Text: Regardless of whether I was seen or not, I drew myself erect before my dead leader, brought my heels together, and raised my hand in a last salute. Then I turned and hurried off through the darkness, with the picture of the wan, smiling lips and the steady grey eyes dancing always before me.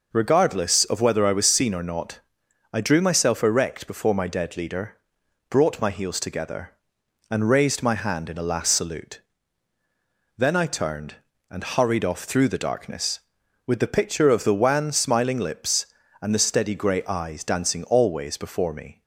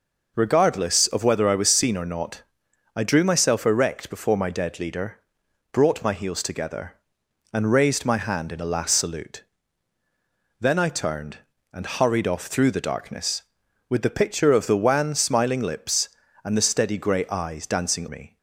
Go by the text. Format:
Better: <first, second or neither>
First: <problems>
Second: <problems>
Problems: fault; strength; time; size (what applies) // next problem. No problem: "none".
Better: first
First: none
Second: skips "always before"; at 18.0 s